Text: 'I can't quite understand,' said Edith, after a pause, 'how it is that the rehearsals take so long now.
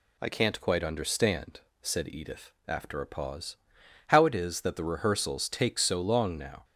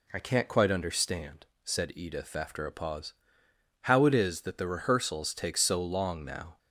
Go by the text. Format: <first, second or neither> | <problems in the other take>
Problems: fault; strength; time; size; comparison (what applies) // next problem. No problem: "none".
neither | none